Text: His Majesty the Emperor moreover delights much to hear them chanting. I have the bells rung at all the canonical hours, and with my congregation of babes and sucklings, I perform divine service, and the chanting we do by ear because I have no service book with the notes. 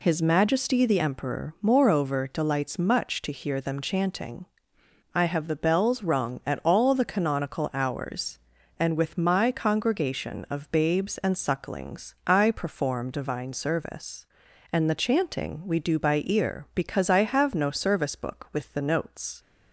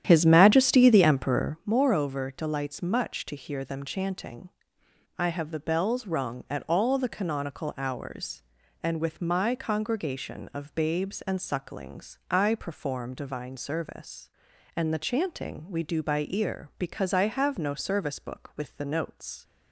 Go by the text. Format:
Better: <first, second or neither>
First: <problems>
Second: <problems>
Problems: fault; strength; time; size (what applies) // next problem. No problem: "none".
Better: first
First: none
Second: starts louder than the rest; strong; until 1.6 s; 10 dB